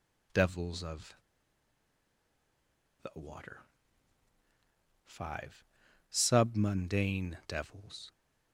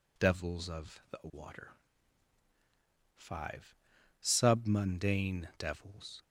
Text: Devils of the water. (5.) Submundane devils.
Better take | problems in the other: second | pauses between "of" and "the"; strong; at 1.1 s; 1.8 s long

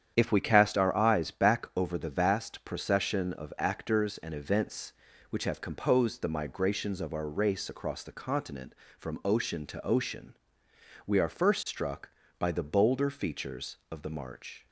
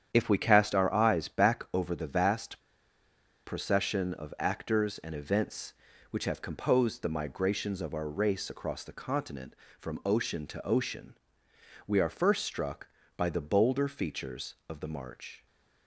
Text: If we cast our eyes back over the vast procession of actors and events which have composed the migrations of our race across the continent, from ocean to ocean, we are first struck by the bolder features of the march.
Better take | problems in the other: first | starts louder than the rest; strong; until 1.1 s; 9 dB; strong in the first // pauses between "vast" and "procession"; noticeable; at 2.6 s; 0.84 s long

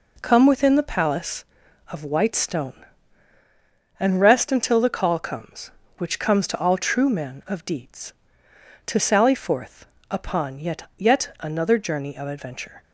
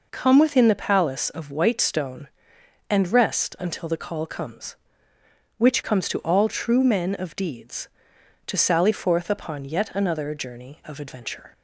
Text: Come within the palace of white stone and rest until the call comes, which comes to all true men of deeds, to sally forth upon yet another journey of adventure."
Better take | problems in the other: second | pauses between "forth" and "upon"; slight; at 9.8 s; 0.24 s long // says "yet" twice; at 10.9 s

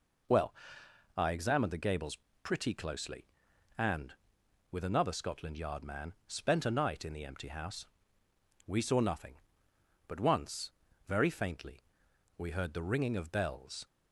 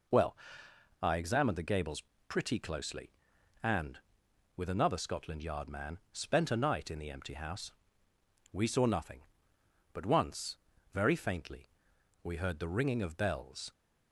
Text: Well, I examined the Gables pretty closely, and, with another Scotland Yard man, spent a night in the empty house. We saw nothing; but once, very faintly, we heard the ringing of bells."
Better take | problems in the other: neither | pauses between "Gables" and "pretty"; slight; the same in both

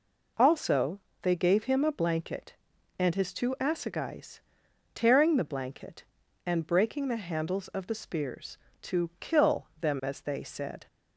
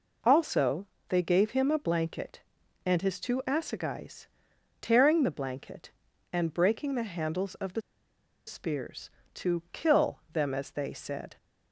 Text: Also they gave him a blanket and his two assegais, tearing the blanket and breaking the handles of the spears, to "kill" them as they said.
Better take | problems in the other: first | pauses between "Also" and "they"; slight; at 0.8 s; 0.22 s long; slight in the first // pauses between "the" and "spears"; noticeable; at 7.8 s; 0.65 s long

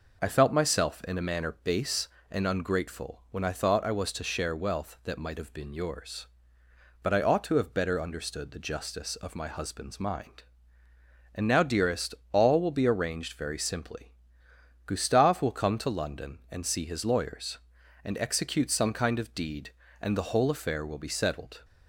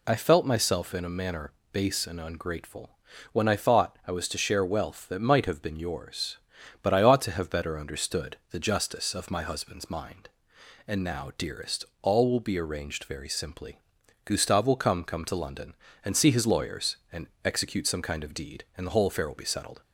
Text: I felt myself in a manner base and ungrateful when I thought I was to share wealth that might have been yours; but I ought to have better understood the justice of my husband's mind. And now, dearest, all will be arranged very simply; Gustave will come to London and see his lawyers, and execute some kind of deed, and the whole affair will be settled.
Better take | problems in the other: first | pauses between "manner" and "base"; slight; at 1.5 s; 0.20 s long // pauses between "ungrateful" and "when"; slight; at 2.9 s; 0.34 s long // says "come" twice; at 15.0 s // pauses between "and" and "execute"; slight; at 17.2 s; 0.16 s long

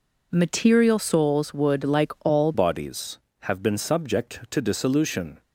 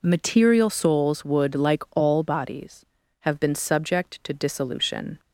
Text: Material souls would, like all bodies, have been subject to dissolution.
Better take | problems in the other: second | changes voice at "bodies"; from 2.5 s on; 2.9 s long

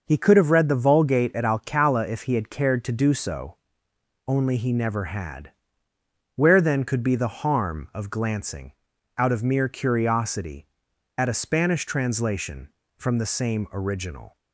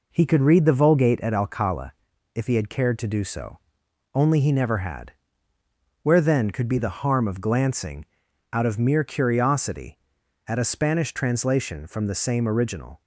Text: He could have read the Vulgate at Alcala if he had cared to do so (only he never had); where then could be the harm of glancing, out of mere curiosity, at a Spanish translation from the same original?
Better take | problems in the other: first | skips "have"; at 0.4 s // pauses between "Alcala" and "if"; at 1.9 s; 0.42 s long

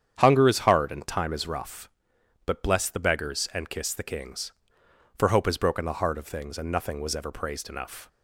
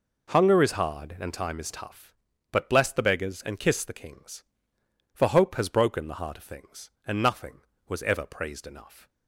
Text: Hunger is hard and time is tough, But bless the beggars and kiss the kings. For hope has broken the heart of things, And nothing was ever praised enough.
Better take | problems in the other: second | starts louder than the rest; strong; until 1.2 s; 8.5 dB // says "rough" for "tough"; at 1.4 s

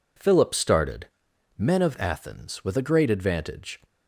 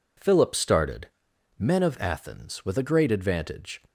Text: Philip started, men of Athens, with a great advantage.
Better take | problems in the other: neither | none

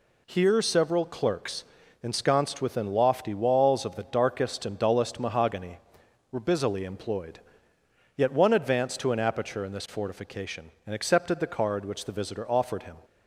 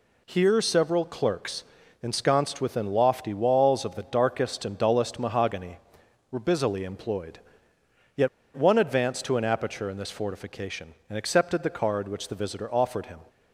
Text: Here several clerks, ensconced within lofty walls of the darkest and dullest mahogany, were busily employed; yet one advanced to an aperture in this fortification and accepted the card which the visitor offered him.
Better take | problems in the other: first | pauses between "yet" and "one"; slight; at 8.2 s; 0.28 s long

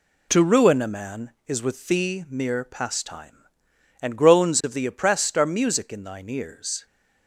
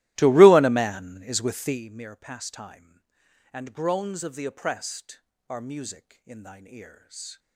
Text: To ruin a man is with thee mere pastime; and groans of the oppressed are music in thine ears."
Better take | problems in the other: first | starts louder than the rest; strong; until 1.9 s; 16 dB

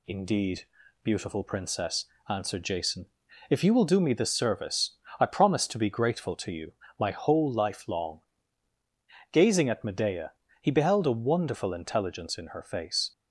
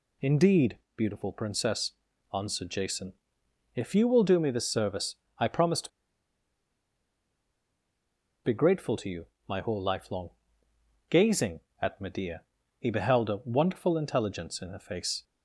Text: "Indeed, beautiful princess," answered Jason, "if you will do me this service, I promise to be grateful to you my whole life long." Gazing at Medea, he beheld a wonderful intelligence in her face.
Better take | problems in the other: first | pauses between "to" and "be"; strong; at 5.8 s; 2.5 s long // pauses between "you" and "my"; slight; at 9.2 s; 0.20 s long; slight in the first

